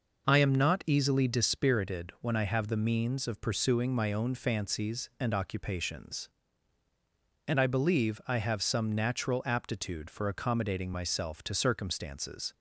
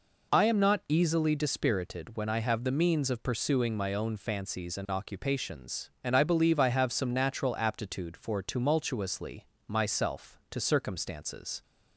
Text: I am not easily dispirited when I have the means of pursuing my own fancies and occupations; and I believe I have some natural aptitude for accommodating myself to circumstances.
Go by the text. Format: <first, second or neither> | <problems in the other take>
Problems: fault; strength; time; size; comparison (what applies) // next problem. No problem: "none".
first | says "tumultuously" for "accommodating"; at 8.4 s